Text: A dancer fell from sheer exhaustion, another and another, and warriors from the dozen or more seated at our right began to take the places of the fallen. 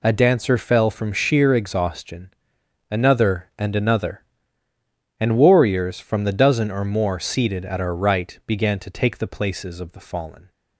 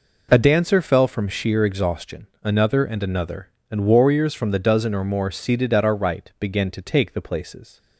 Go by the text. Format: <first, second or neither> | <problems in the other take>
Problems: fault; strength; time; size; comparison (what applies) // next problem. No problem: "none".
first | stops before "of the fallen"; at 7.7 s